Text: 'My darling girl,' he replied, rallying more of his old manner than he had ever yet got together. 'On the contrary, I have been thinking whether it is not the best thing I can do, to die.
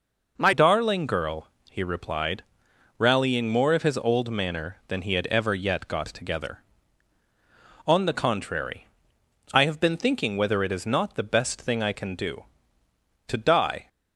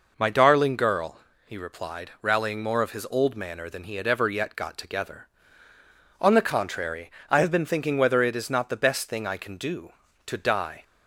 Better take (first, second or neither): second